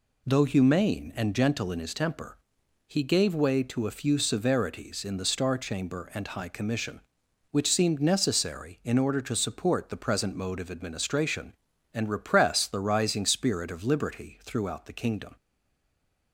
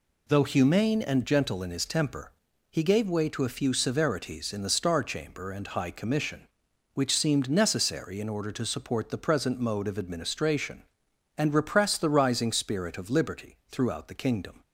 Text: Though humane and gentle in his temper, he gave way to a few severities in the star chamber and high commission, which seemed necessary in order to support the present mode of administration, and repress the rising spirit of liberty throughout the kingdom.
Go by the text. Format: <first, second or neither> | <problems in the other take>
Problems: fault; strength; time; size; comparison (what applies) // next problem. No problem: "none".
second | stays silent after the last word; from 15.3 s on; 1.0 s long